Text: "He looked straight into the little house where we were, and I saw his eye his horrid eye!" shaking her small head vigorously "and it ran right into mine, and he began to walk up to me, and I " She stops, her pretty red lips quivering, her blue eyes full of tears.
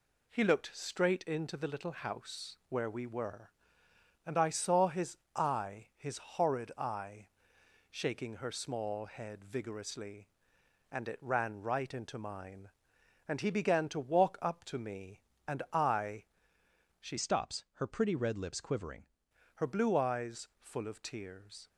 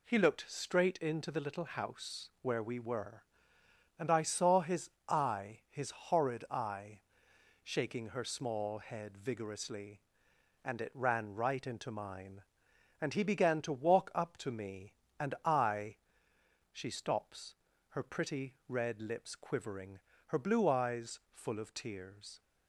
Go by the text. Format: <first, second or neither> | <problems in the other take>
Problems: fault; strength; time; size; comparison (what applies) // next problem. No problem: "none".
second | pauses between "his" and "eye"; slight; at 5.1 s; 0.18 s long; slight in the second // changes voice from "stops" to "quivering"; from 17.1 to 19.0 s; 1.9 s long